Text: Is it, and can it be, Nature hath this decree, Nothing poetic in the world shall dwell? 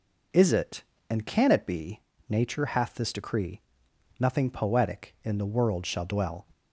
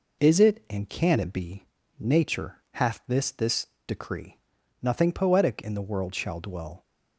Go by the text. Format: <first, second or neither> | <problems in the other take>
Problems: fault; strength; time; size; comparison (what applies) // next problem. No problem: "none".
first | pauses between "Nature" and "hath"; slight; at 2.5 s; 0.16 s long // says "this" twice; at 3.2 s